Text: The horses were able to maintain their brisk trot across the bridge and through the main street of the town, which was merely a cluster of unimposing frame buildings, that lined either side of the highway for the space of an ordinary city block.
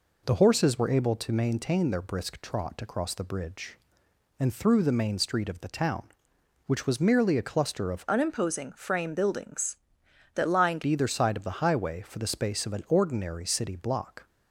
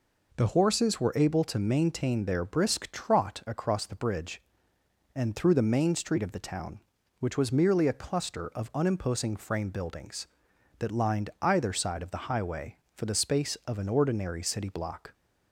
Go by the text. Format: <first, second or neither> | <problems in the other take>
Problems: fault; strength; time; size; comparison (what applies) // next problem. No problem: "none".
second | changes voice from "unimposing" to "lined"; from 8.0 to 10.8 s; 2.8 s long